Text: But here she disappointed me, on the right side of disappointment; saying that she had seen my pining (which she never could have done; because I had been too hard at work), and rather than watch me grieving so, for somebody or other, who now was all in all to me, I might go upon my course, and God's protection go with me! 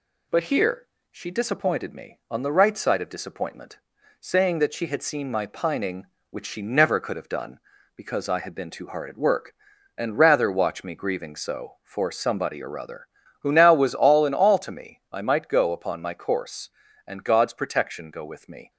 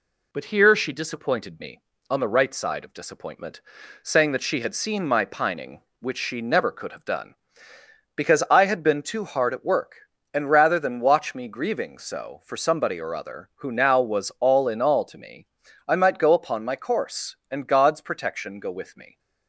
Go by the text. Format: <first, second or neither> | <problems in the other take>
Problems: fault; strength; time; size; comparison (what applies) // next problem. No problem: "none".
second | pauses between "here" and "she"; slight; at 0.8 s; 0.26 s long // skips "than"; at 10.5 s